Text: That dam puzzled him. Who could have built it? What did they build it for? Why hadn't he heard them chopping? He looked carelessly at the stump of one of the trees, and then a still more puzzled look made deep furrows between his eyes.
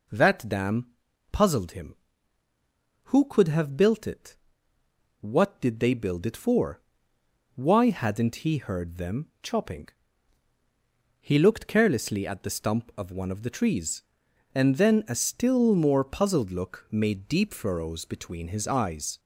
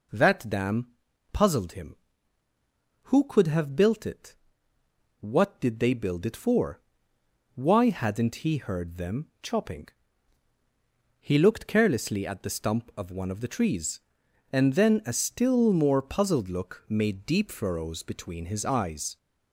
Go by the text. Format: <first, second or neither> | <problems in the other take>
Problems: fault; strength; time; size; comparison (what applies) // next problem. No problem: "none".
neither | pauses between "dam" and "puzzled"; noticeable; the same in both